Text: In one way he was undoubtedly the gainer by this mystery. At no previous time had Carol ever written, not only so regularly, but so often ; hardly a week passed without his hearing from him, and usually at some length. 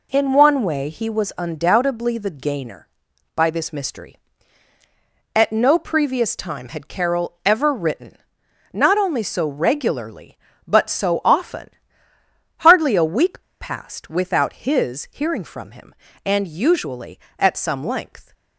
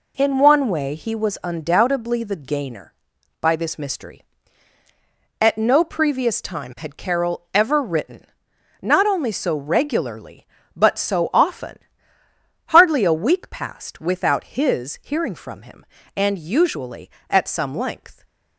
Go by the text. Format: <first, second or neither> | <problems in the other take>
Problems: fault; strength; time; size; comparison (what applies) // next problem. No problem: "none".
second | pauses between "week" and "passed"; slight; at 13.4 s; 0.20 s long